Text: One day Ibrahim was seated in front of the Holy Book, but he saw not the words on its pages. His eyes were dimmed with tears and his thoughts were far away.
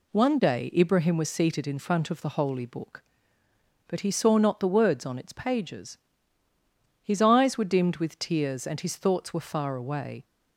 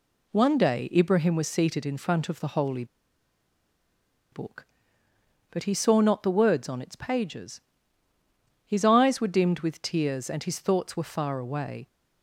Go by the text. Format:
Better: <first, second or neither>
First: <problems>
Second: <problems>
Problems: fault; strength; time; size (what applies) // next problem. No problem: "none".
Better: first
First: none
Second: pauses between "Holy" and "Book"; strong; at 2.8 s; 1.4 s long